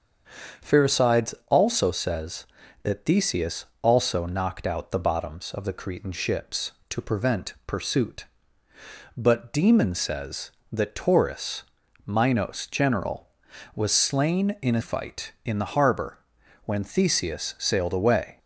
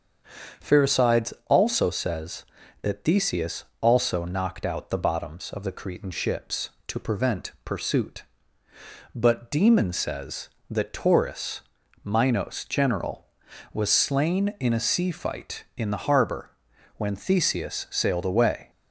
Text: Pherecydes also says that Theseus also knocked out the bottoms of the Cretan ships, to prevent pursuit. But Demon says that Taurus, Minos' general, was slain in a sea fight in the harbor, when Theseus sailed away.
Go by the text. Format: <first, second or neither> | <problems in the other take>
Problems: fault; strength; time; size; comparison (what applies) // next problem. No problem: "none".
second | starts louder than the rest; strong; until 1.7 s; 7 dB; strong in the second // pauses between "Theseus" and "also"; slight; at 3.6 s; 0.16 s long; slight in the second // skips "sea"; at 14.8 s